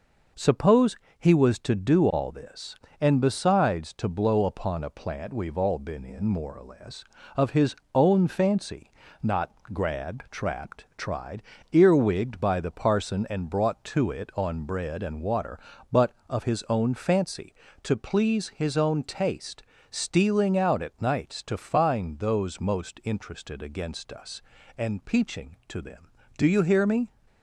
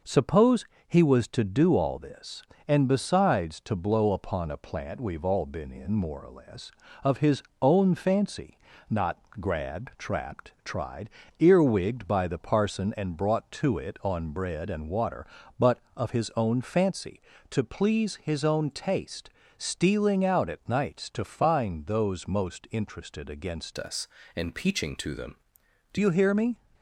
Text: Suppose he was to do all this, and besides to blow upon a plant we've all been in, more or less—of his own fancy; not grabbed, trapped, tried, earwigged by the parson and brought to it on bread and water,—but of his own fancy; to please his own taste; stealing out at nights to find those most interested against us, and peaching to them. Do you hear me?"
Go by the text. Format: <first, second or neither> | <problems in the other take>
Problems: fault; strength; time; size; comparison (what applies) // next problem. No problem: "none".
first | pauses between "Suppose" and "he"; slight; at 0.6 s; 0.22 s long; slight in the first // pauses between "his" and "own"; slight; at 7.4 s; 0.18 s long; slight in the first // pauses between "not" and "grabbed"; slight; at 9.1 s; 0.20 s long; slight in the first // changes voice from "us" to "Do"; from 23.7 to 25.9 s; 2.2 s long